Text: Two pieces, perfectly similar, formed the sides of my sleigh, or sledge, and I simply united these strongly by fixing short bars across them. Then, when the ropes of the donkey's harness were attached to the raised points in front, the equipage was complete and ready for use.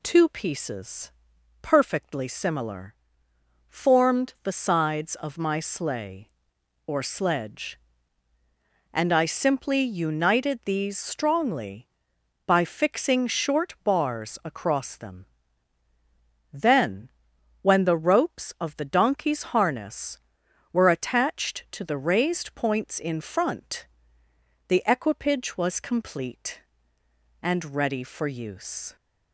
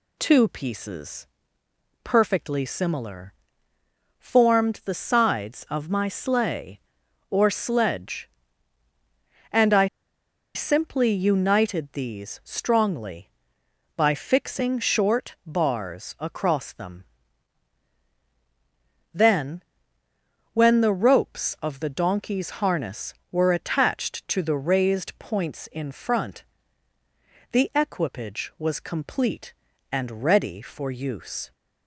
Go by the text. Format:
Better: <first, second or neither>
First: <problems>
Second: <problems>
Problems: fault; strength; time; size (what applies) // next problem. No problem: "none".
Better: first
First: none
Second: pauses between "I" and "simply"; noticeable; at 9.8 s; 0.69 s long